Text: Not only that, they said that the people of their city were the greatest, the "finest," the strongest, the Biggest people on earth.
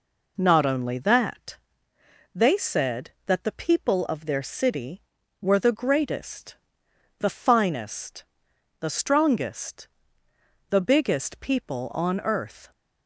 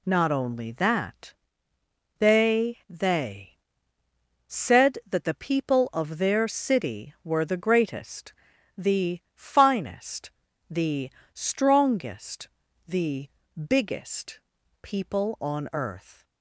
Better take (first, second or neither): first